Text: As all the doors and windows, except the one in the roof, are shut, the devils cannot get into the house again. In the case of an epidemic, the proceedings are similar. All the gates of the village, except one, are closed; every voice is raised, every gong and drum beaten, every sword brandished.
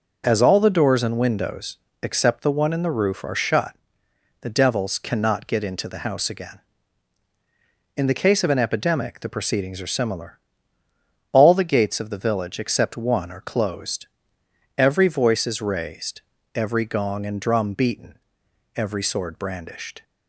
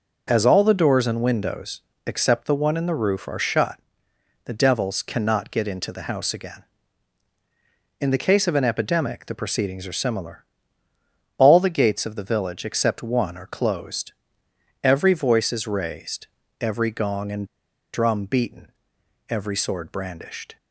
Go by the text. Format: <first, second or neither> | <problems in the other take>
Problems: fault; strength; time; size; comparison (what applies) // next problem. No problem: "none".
first | pauses between "and" and "drum"; noticeable; at 17.4 s; 0.47 s long